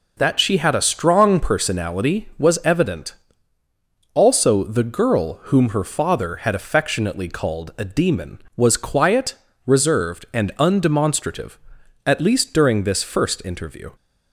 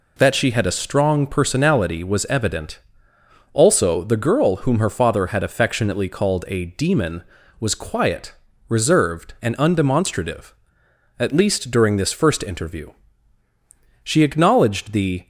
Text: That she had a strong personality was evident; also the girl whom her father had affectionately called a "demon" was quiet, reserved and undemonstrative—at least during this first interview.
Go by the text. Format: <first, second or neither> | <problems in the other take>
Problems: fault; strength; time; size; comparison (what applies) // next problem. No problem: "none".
first | goes on to say "She acknowledged the"; noticeable; from 14.0 s on; 1.2 s long